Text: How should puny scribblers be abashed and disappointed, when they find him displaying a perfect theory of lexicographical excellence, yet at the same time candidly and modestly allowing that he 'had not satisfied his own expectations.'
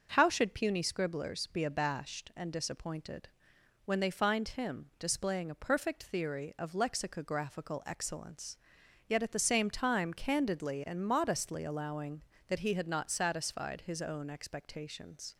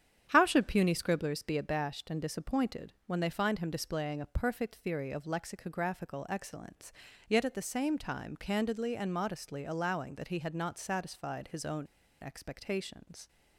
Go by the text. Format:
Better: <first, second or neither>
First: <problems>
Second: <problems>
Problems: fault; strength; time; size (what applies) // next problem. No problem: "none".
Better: first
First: starts louder than the rest; until 1.1 s; 6 dB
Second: starts louder than the rest; strong; until 1.3 s; 9 dB // pauses between "own" and "expectations"; slight; at 11.8 s; 0.35 s long